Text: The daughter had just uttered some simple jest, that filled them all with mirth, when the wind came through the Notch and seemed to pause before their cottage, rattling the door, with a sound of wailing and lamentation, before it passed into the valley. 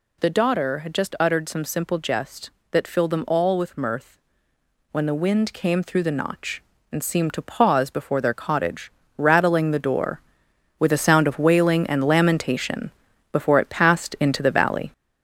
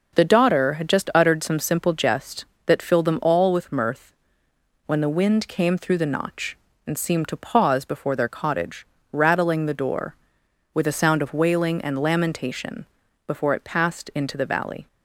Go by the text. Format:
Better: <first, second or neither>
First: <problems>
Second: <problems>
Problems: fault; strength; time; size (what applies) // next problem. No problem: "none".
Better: second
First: gets louder; noticeable; throughout; 5 dB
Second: none